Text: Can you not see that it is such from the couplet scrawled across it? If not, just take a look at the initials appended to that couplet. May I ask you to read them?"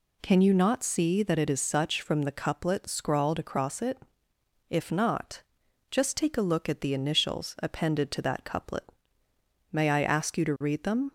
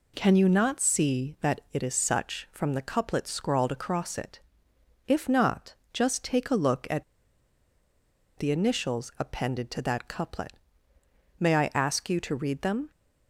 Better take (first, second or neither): first